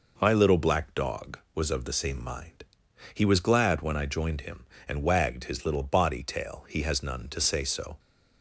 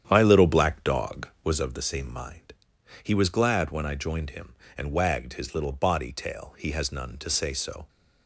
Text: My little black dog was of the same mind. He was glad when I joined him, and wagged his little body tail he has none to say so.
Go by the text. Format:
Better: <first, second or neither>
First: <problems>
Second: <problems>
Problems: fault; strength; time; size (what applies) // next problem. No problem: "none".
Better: first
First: none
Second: starts louder than the rest; strong; until 1.7 s; 9.5 dB